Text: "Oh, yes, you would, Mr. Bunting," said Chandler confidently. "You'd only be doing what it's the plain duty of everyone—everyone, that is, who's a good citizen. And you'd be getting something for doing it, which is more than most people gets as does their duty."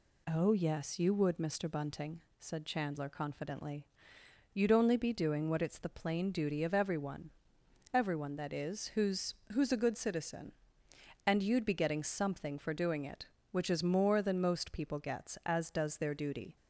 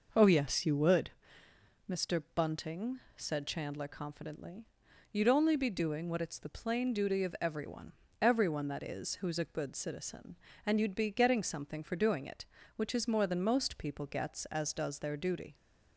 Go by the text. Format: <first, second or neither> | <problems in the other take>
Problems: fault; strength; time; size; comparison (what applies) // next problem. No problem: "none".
second | says "who's" twice; at 9.5 s